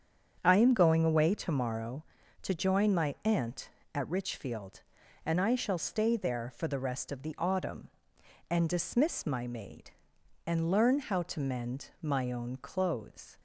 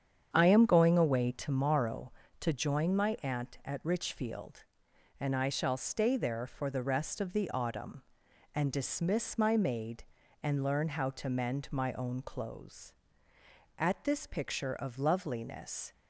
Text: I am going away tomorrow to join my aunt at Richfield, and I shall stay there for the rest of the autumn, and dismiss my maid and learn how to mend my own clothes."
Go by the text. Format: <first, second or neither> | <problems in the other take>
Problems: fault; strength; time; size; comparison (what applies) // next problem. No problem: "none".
first | starts louder than the rest; strong; until 1.3 s; 8 dB; strong in the first // goes on to say "At this picture of loveliness"; strong; from 13.7 s on; 2.1 s long